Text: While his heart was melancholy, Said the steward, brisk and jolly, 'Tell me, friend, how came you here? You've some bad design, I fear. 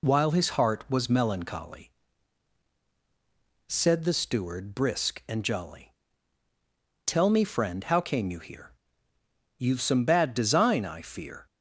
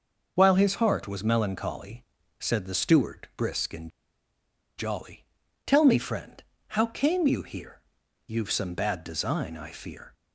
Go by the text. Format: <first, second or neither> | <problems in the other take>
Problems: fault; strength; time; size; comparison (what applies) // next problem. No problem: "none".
first | pauses between "and" and "jolly"; noticeable; at 3.8 s; 0.88 s long